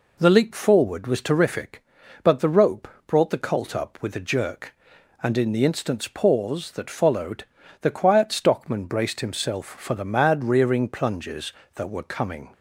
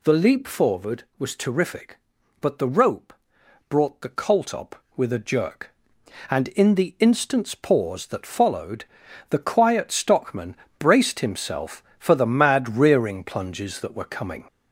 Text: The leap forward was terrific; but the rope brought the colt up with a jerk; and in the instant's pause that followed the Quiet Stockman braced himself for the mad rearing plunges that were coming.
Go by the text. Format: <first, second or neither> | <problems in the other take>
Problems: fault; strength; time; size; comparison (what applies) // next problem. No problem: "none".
first | gets louder; throughout; 4 dB // pauses between "rope" and "brought"; noticeable; at 3.1 s; 0.56 s long; slight in the first // pauses between "followed" and "the"; noticeable; at 8.8 s; 0.46 s long; also in the first // pauses between "Stockman" and "braced"; slight; at 10.5 s; 0.24 s long